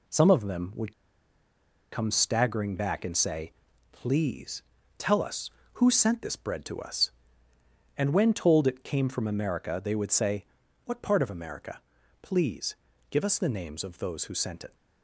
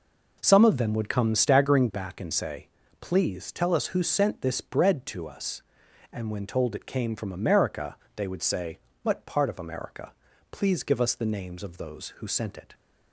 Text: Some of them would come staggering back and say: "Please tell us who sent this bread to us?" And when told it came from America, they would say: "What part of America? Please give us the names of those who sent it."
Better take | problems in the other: second | pauses between "would" and "come"; at 0.9 s; 0.99 s long // pauses between "Please" and "tell"; slight; at 4.6 s; 0.34 s long // pauses between "Please" and "give"; slight; at 12.7 s; 0.36 s long

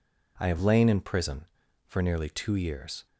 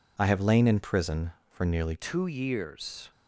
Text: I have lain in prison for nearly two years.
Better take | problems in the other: first | changes voice at "two"; from 1.9 s on; 1.2 s long

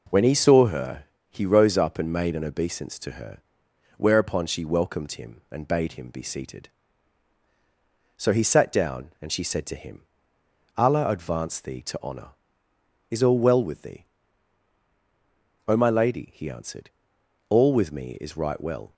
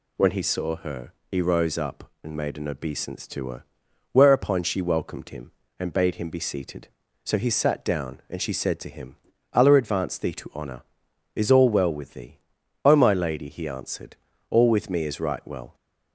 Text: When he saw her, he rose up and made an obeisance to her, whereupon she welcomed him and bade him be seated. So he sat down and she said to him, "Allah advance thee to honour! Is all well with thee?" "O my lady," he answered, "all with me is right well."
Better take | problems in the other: neither | none

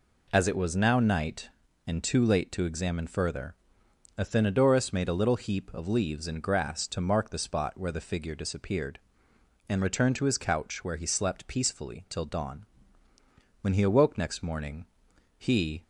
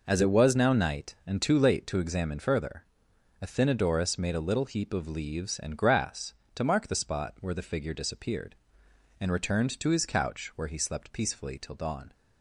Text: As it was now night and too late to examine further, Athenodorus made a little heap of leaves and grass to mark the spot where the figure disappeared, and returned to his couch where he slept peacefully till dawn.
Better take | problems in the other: second | goes on to say "When he awoke next morning he"; strong; from 13.6 s on; 2.2 s long

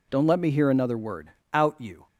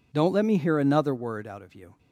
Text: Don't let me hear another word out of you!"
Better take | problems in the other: second | pauses between "word" and "out"; slight; at 1.3 s; 0.22 s long // skips "of"; at 1.8 s

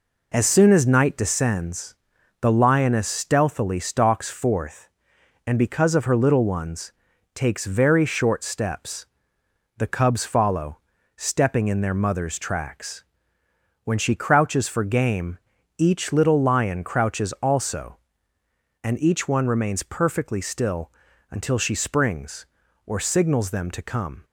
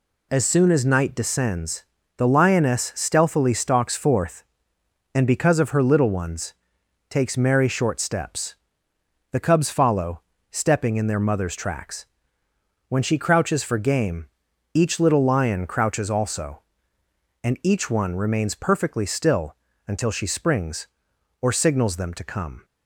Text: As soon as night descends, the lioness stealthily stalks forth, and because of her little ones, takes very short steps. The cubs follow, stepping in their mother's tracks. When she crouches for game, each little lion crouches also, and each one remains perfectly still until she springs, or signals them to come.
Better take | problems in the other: first | says "merry" for "very"; at 7.3 s // pauses between "still" and "until"; slight; at 19.5 s; 0.32 s long; also in the first

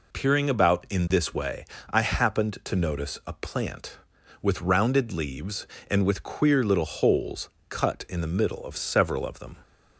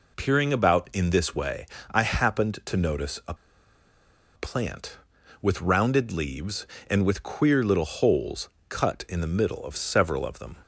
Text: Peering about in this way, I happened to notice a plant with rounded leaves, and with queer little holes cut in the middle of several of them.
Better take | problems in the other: first | pauses between "a" and "plant"; at 3.3 s; 1.0 s long // pauses between "holes" and "cut"; slight; at 8.4 s; 0.20 s long; slight in the first

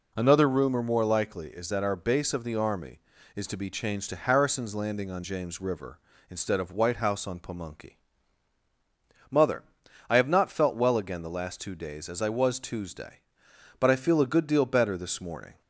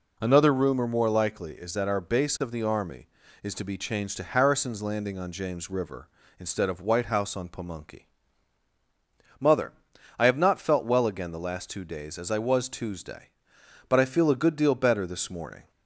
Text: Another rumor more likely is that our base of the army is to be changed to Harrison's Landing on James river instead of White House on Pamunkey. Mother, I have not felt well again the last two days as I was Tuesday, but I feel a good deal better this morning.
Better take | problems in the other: neither | none

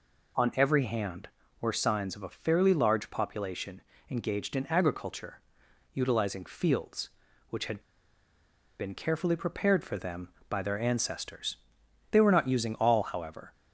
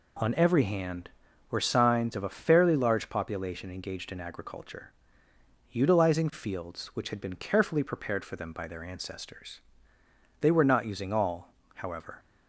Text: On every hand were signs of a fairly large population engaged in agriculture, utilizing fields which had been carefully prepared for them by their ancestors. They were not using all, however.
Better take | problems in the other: second | pauses between "population" and "engaged"; slight; at 3.7 s; 0.30 s long // pauses between "had" and "been"; at 7.7 s; 0.98 s long

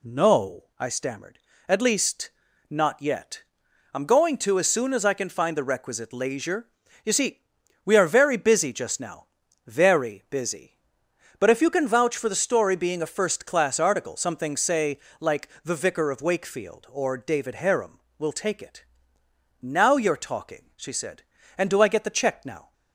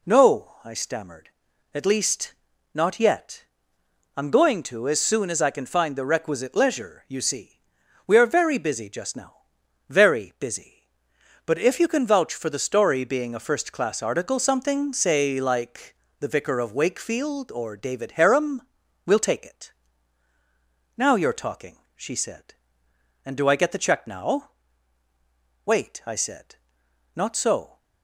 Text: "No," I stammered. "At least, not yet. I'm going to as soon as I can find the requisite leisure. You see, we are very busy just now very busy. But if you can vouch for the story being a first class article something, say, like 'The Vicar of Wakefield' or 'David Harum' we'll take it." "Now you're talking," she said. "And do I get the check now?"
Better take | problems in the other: first | pauses between "now" and "very"; noticeable; at 9.3 s; 0.52 s long; also in the first // pauses between "like" and "The"; slight; at 15.9 s; 0.24 s long; slight in the first // pauses between "Harum" and "we'll"; at 18.6 s; 0.42 s long; slight in the first // goes on to say "Wait I said not so"; strong; from 25.6 s on; 2.1 s long

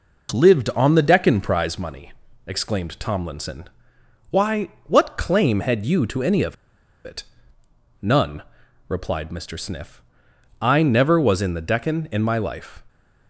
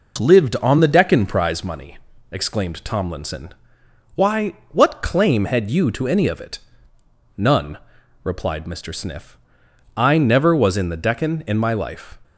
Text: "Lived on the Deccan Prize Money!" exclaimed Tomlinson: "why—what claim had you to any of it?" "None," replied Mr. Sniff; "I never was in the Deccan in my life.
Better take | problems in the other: second | pauses between "of" and "it"; noticeable; at 6.5 s; 0.50 s long

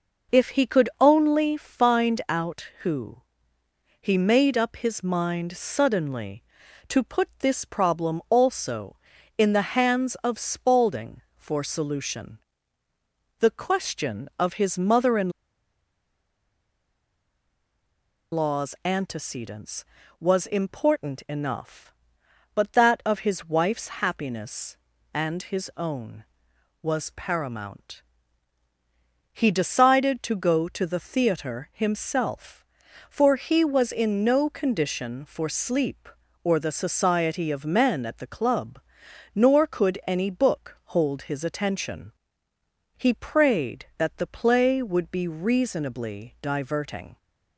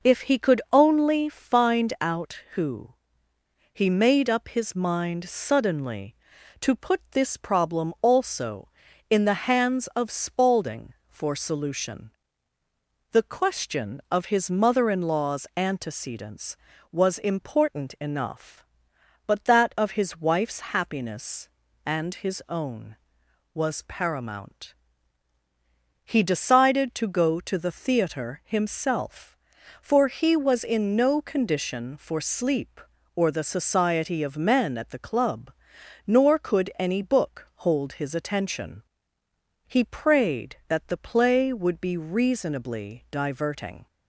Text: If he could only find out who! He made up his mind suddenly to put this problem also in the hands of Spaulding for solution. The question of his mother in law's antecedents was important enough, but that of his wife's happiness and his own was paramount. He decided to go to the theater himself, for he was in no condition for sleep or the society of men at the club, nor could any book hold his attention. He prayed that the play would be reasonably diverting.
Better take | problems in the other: second | pauses between "in" and "law's"; strong; at 15.2 s; 3.0 s long

